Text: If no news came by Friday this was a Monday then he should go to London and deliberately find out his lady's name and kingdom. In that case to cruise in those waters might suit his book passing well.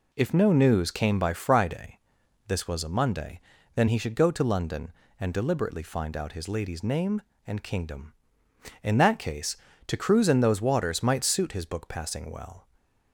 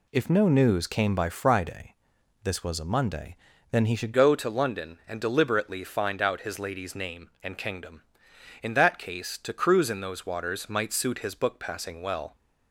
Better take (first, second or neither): first